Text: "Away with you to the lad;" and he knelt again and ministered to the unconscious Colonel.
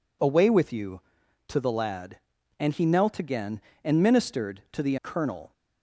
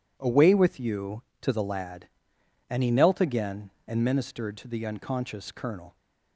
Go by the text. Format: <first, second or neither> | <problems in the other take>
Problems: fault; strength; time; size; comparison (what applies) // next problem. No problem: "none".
second | skips "unconscious"; at 4.9 s